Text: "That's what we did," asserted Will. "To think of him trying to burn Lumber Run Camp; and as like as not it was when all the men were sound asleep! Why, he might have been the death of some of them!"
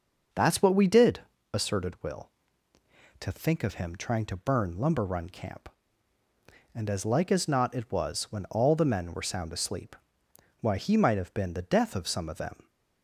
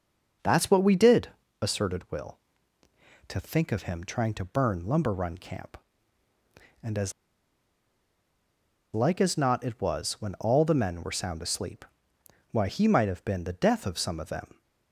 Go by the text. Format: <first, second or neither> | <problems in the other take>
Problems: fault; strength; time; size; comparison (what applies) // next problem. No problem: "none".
first | starts louder than the rest; until 1.7 s; 6 dB; also in the first // pauses between "as" and "like"; strong; at 7.1 s; 1.8 s long